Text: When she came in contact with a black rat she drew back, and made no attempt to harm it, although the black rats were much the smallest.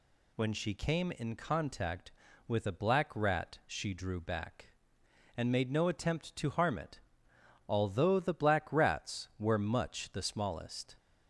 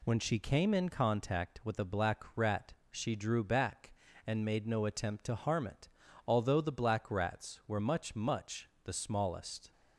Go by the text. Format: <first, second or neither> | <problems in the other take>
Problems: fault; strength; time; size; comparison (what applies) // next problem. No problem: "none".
first | pauses between "rat" and "she"; slight; at 2.7 s; 0.18 s long // says "much" twice; at 8.1 s